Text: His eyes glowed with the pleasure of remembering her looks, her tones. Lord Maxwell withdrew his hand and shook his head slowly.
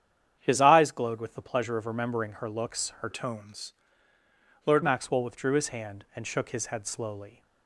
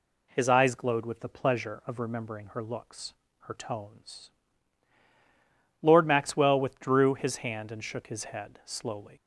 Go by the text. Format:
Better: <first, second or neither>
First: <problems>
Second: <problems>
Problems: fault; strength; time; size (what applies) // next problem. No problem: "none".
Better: second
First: starts louder than the rest; strong; until 1.3 s; 8.5 dB // changes voice from "tones" to "Lord"; from 3.1 to 4.8 s; 1.7 s long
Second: none